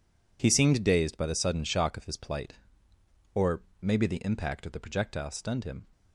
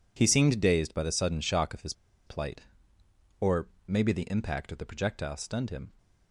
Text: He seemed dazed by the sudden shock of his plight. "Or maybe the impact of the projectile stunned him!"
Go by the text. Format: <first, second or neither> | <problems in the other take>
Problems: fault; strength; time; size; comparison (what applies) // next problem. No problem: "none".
first | pauses between "his" and "plight"; slight; at 1.9 s; 0.33 s long // pauses between "Or" and "maybe"; slight; at 3.6 s; 0.18 s long; slight in the first